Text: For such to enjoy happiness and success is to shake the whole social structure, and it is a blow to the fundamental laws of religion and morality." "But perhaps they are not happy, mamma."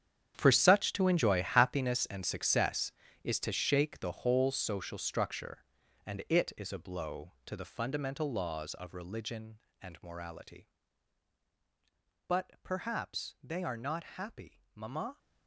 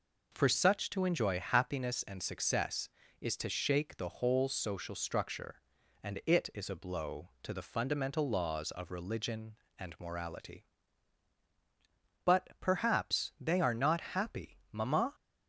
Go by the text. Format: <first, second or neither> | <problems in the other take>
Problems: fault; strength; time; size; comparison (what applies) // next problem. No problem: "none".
second | gets quieter; strong; throughout; 15 dB